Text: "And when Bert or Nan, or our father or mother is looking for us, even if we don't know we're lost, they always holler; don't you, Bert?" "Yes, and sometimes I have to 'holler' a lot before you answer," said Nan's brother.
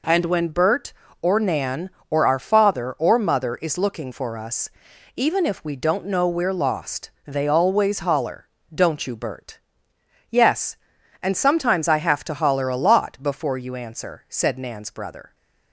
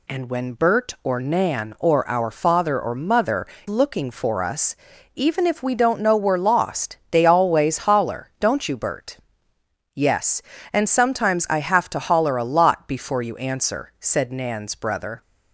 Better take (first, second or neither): first